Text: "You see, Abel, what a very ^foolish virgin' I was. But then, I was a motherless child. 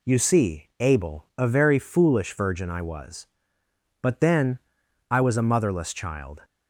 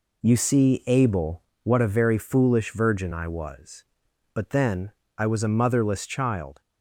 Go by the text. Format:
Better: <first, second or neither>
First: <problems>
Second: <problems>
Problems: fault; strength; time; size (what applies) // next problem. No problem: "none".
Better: second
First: skips "what"; at 1.3 s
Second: none